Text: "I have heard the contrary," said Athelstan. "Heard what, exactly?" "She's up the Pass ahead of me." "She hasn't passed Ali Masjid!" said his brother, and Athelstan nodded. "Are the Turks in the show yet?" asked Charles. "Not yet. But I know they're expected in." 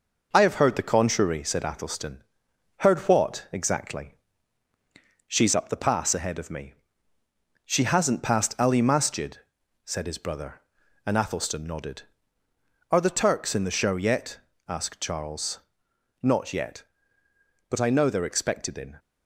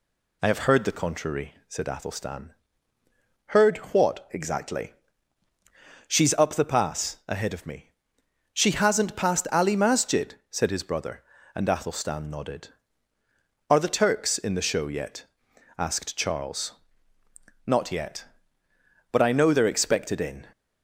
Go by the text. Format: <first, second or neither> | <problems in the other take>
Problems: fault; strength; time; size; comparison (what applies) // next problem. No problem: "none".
second | gets quieter; slight; throughout; 3 dB